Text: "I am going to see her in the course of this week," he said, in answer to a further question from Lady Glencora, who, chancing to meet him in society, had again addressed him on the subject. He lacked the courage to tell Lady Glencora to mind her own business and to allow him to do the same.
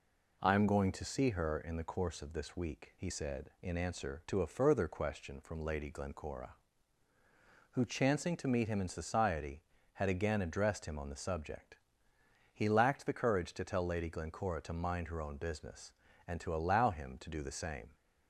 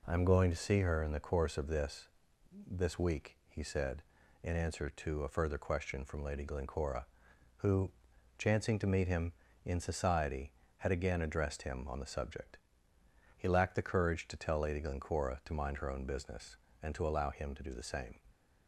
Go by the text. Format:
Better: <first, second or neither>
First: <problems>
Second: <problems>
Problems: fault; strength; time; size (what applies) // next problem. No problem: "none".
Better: first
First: none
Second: says "this" twice; at 2.6 s